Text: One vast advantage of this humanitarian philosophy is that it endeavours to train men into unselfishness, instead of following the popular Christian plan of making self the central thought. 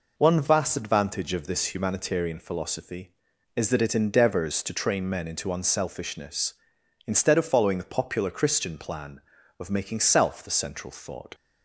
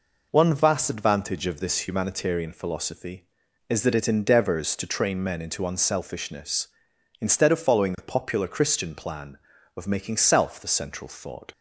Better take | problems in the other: neither | none

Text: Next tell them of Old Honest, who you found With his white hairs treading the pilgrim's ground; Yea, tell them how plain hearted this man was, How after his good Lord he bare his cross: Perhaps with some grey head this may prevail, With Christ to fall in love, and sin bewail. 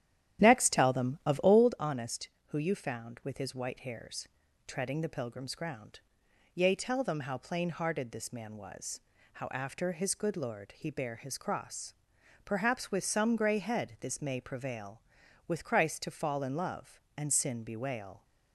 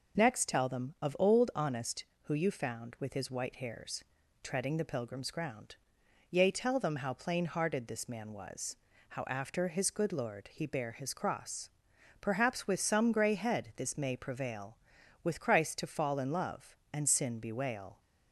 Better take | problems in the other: second | starts louder than the rest; strong; until 1.7 s; 11.5 dB // pauses between "hairs" and "treading"; at 4.2 s; 0.40 s long; also in the second

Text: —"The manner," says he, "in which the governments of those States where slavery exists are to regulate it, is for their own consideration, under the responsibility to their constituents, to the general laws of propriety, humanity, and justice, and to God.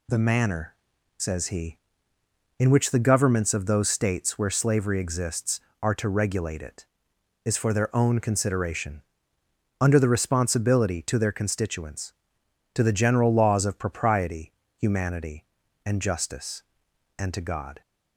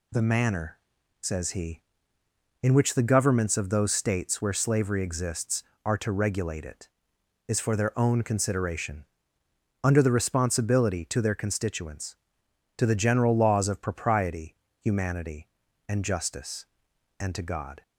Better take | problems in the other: neither | none

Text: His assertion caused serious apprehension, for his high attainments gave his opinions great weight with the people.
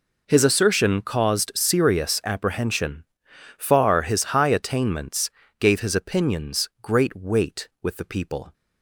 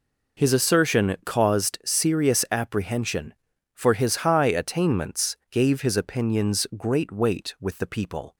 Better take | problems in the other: second | says "far" for "for"; at 3.5 s // pauses between "attainments" and "gave"; slight; at 5.3 s; 0.28 s long

